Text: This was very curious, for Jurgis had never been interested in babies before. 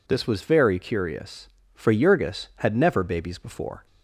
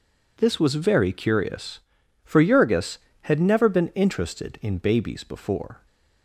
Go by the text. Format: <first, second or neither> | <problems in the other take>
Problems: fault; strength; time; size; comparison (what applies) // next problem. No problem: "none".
second | skips "been interested in"; at 3.0 s